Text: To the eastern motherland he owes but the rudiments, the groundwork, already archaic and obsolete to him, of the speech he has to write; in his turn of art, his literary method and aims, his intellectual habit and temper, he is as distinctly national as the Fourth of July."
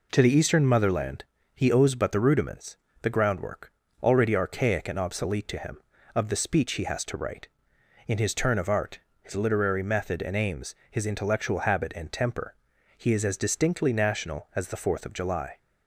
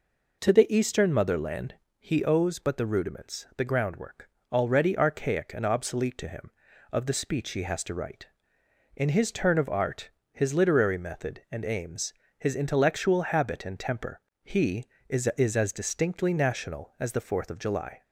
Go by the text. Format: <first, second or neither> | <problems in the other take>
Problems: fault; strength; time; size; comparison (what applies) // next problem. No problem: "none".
first | pauses between "motherland" and "he"; slight; at 1.7 s; 0.24 s long; slight in the first // says "is" twice; at 15.3 s